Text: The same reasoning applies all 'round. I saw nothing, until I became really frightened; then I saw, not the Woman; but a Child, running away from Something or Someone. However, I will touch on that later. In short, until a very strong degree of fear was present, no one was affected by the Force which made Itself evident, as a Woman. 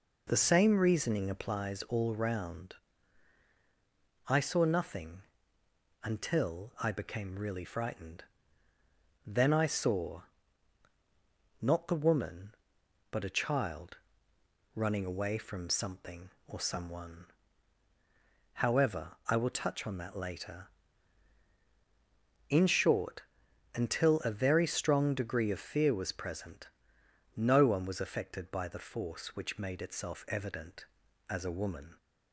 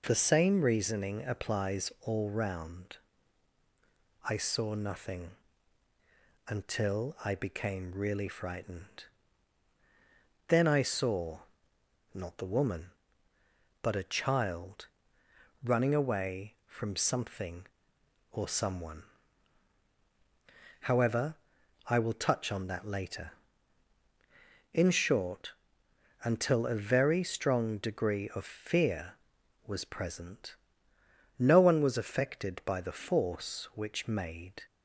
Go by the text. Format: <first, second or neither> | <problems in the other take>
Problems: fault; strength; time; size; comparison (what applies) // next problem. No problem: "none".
first | stops before "Itself evident as a Woman"; at 34.6 s